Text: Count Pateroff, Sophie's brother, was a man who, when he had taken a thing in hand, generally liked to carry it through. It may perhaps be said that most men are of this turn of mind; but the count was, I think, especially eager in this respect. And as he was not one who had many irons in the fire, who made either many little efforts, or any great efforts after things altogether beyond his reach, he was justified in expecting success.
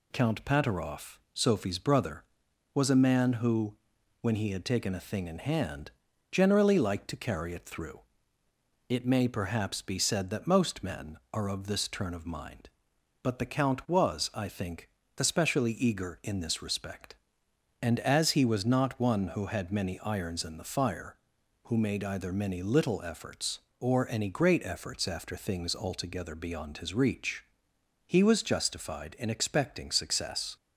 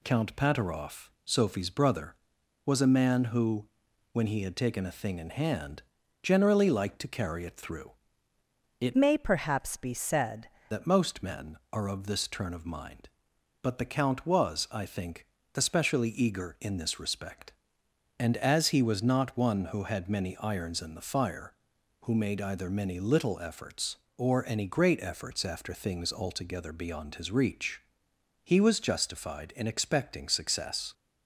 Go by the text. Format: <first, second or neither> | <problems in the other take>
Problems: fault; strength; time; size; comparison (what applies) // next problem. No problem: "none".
first | changes voice from "may" to "said"; from 8.9 to 10.4 s; 1.5 s long